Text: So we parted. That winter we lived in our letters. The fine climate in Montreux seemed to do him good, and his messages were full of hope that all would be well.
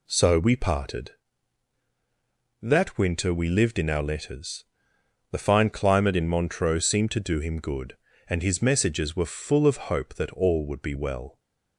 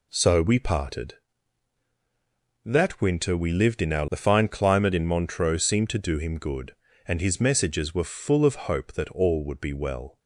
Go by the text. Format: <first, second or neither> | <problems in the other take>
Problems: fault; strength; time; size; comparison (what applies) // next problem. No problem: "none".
first | skips "letters"; at 4.0 s